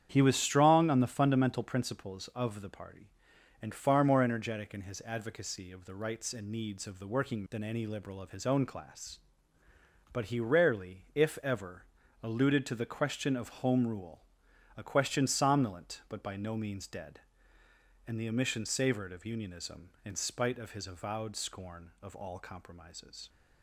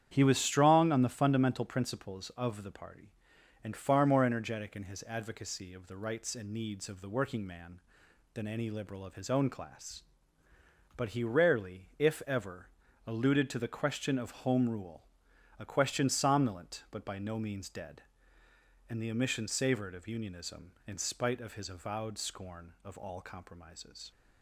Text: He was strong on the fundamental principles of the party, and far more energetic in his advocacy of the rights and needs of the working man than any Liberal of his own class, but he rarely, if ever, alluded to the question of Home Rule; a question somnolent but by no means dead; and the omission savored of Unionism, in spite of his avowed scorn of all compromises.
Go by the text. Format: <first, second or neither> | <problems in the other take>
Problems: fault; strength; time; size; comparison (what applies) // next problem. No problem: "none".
second | starts louder than the rest; strong; until 1.1 s; 9 dB; strong in the second // skips "man"; at 7.4 s